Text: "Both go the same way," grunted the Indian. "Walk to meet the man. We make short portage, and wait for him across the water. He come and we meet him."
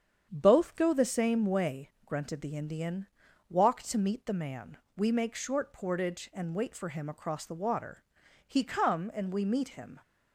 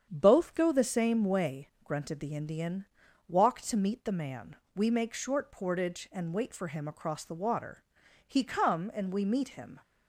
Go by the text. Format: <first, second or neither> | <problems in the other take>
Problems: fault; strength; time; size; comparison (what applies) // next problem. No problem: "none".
neither | starts louder than the rest; strong; the same in both